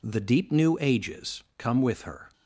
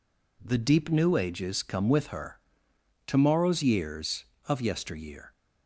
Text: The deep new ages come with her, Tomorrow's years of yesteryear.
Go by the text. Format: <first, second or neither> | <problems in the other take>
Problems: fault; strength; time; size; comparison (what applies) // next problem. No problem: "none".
second | stops before "Tomorrow's years of yesteryear"; at 2.3 s